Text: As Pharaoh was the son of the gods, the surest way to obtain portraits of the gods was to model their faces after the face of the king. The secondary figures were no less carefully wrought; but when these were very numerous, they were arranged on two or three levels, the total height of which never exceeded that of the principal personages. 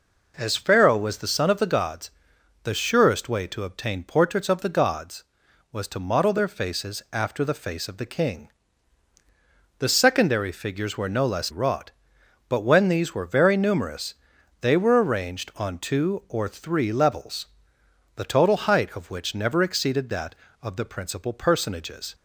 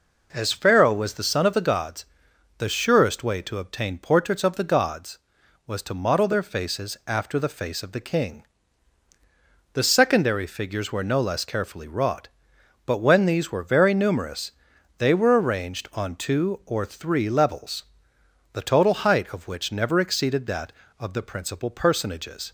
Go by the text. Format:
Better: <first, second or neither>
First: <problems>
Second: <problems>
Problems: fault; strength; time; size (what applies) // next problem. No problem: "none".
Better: second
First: skips "carefully"; at 11.4 s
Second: none